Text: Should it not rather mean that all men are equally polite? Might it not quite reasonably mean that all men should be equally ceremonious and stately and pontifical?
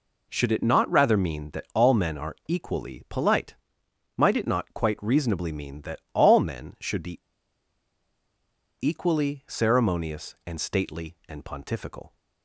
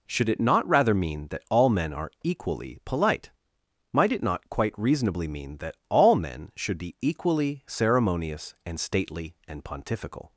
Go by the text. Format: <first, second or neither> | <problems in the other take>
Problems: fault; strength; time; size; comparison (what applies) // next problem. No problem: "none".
second | pauses between "be" and "equally"; strong; at 7.1 s; 1.6 s long